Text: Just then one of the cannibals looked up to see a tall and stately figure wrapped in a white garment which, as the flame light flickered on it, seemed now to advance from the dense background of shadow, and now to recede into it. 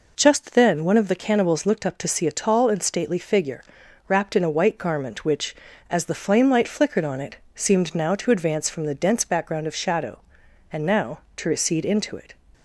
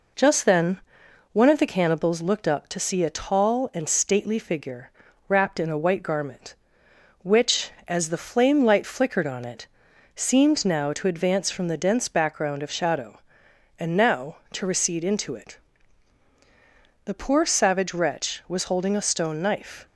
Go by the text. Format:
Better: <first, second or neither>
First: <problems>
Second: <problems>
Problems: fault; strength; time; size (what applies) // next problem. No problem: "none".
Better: first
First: pauses between "figure" and "wrapped"; noticeable; at 3.6 s; 0.46 s long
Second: pauses between "then" and "one"; noticeable; at 0.7 s; 0.52 s long // pauses between "figure" and "wrapped"; at 4.8 s; 0.38 s long // goes on to say "The poor savage wretch was holding a stone knife"; strong; from 17.0 s on; 2.8 s long